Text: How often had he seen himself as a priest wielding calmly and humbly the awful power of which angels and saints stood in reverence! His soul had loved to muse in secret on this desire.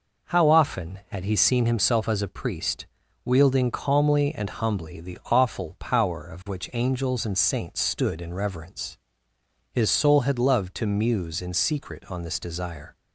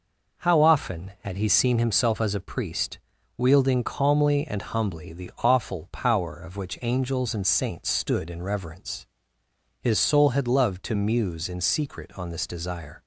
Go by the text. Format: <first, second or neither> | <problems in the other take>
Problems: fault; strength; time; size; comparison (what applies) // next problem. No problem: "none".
neither | pauses between "priest" and "wielding"; the same in both